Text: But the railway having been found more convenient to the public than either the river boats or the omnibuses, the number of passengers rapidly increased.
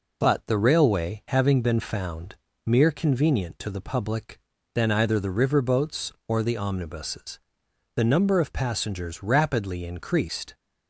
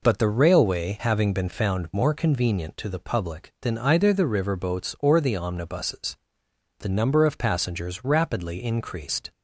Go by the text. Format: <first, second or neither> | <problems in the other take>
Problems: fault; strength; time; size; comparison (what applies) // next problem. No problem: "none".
second | says "mere" for "more"; at 2.6 s